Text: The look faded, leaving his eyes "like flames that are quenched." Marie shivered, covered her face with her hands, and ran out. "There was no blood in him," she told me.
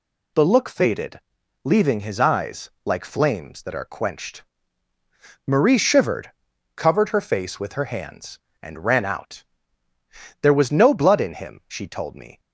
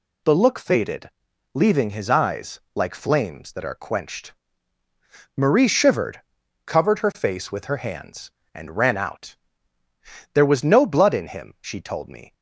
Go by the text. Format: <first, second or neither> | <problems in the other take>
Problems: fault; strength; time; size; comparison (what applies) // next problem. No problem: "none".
neither | none